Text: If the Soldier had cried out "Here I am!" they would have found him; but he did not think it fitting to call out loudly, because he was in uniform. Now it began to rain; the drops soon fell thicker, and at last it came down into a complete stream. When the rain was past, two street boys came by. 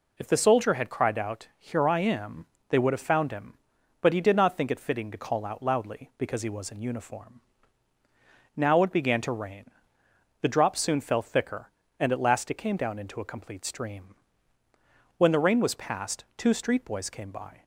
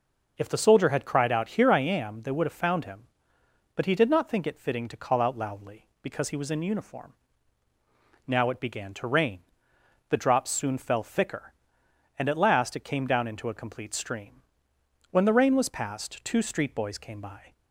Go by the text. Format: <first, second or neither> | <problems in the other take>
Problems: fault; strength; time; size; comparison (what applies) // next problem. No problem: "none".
neither | none